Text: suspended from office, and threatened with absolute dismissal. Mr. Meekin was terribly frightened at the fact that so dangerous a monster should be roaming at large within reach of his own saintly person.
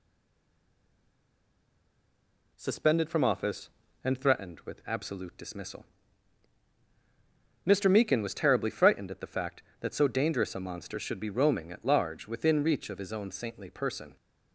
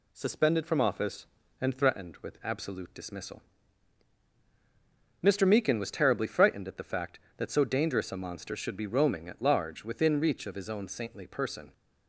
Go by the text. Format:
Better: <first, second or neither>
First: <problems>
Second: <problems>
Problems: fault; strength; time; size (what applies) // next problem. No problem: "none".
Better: second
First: stays silent before the first word; strong; until 2.5 s; 2.5 s long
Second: none